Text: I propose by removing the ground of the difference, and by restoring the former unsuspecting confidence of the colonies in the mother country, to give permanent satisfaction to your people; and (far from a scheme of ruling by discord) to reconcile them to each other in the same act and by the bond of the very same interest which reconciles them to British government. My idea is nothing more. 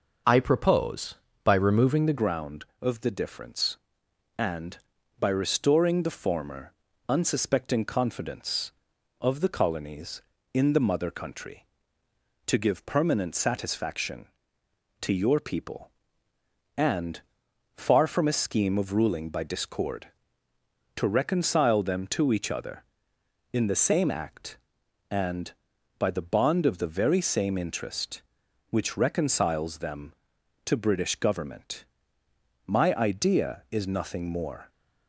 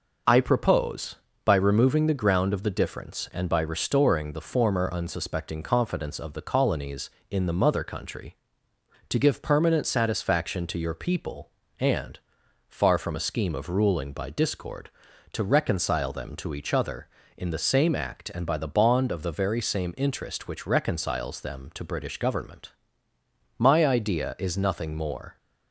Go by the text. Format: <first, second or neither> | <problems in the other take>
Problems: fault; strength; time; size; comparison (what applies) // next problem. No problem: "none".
second | changes voice at "ground"; from 2.1 s on; 32.5 s long // pauses between "former" and "unsuspecting"; slight; at 6.7 s; 0.34 s long